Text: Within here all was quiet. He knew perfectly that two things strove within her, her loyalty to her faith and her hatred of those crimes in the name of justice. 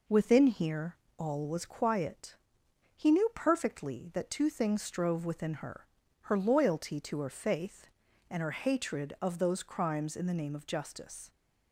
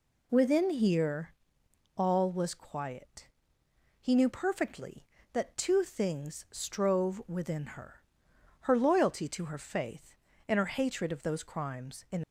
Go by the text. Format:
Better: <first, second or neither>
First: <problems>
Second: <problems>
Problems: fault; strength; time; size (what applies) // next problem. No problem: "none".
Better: first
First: pauses between "here" and "all"; slight; at 0.9 s; 0.24 s long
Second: pauses between "here" and "all"; noticeable; at 1.3 s; 0.64 s long // stops before "the name of justice"; at 12.2 s